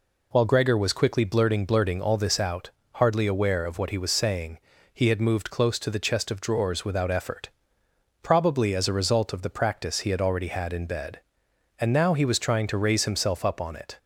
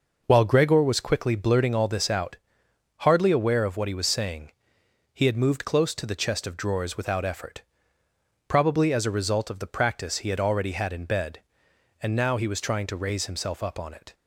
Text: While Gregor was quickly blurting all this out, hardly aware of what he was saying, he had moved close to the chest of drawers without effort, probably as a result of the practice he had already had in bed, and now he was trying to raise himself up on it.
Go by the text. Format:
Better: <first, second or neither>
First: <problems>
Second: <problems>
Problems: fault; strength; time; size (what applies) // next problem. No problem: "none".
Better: second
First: says "blurting" twice; at 1.6 s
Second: none